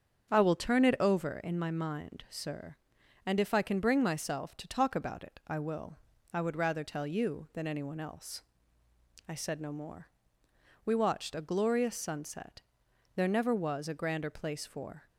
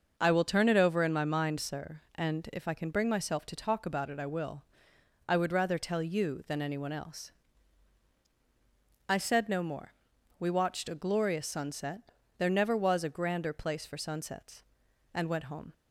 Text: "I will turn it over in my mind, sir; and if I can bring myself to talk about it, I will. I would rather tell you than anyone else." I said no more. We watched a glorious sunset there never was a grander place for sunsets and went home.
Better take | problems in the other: second | starts louder than the rest; strong; until 1.3 s; 7.5 dB; noticeable in the second // pauses between "sunset" and "there"; noticeable; at 12.5 s; 0.56 s long; slight in the second // stops before "sunsets and went home"; at 15.0 s

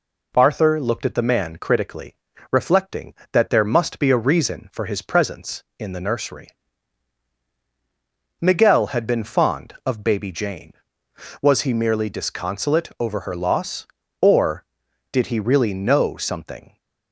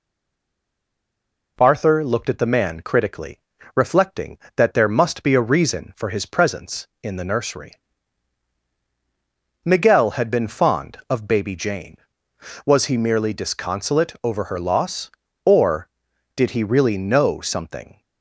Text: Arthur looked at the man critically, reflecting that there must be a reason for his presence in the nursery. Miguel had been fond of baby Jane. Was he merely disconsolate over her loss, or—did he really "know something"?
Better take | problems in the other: first | stays silent before the first word; noticeable; until 1.5 s; 1.5 s long

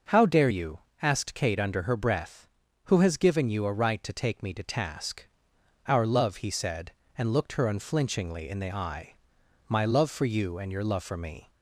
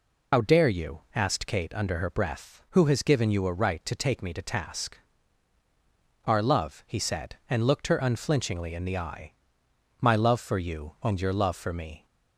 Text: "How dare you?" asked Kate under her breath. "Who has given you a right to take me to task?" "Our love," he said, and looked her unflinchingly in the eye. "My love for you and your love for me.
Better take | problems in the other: first | loses the start of "How"; at 0.3 s; 70 ms

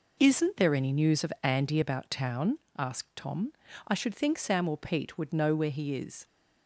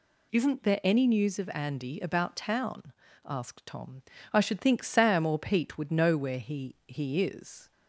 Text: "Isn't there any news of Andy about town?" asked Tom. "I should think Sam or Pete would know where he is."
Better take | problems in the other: first | says "he" twice; at 6.8 s

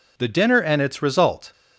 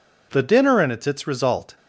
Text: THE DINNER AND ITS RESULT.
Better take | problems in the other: first | says "ITS" twice; at 1.0 s

